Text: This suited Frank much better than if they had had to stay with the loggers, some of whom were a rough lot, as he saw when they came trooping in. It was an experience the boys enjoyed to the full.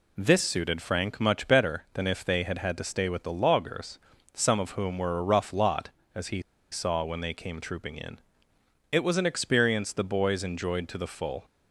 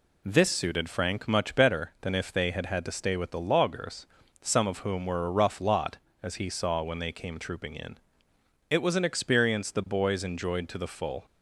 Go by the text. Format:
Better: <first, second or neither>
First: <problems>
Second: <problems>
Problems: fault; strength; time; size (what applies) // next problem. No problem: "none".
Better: second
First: pauses between "he" and "saw"; slight; at 6.3 s; 0.32 s long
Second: none